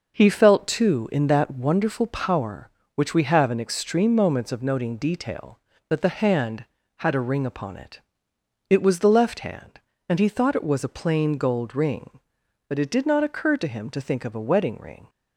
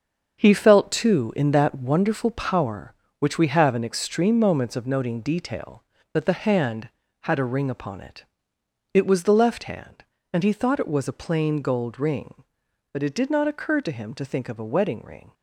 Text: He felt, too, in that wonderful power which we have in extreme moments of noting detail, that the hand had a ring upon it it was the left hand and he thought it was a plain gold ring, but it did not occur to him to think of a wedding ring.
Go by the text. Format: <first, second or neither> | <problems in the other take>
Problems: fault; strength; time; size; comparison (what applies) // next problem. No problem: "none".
first | gets quieter; strong; throughout; 9.5 dB // pauses between "it" and "it"; noticeable; at 8.2 s; 0.70 s long; noticeable in the first